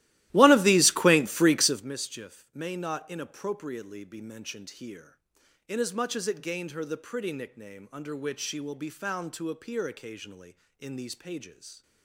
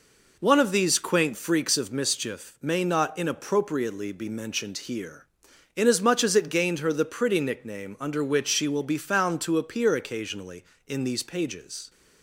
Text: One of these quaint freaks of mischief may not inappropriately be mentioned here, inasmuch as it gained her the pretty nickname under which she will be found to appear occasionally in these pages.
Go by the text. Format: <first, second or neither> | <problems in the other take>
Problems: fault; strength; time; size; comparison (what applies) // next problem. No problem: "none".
second | starts louder than the rest; strong; until 1.9 s; 16.5 dB